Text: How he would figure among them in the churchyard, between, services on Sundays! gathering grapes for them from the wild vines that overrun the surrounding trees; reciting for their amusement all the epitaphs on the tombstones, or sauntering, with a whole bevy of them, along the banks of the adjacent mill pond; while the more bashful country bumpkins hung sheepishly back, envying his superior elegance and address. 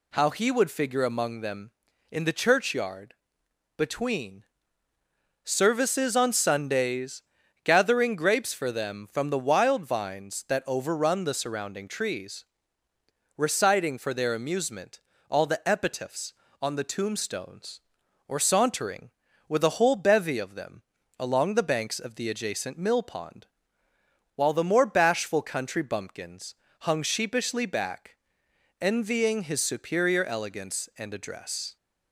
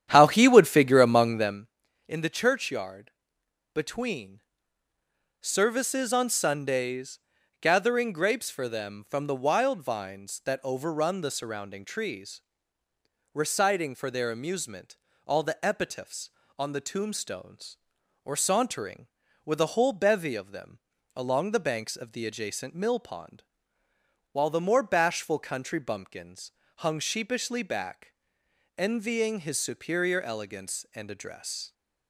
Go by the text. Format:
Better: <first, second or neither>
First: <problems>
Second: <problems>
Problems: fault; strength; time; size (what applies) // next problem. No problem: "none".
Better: first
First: pauses between "amusement" and "all"; slight; at 14.9 s; 0.32 s long // pauses between "bumpkins" and "hung"; slight; at 26.5 s; 0.26 s long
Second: starts louder than the rest; strong; until 1.7 s; 10 dB // pauses between "amusement" and "all"; slight; at 14.9 s; 0.32 s long // pauses between "bumpkins" and "hung"; slight; at 26.5 s; 0.26 s long